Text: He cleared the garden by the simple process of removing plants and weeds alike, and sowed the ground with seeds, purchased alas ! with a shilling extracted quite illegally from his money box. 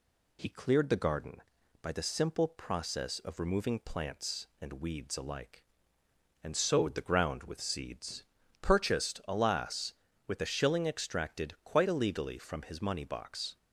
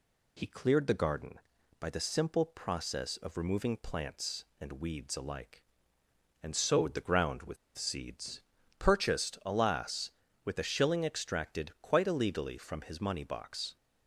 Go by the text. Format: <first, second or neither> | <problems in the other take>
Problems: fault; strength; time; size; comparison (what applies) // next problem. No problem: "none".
first | pauses between "with" and "seeds"; slight; at 7.5 s; 0.21 s long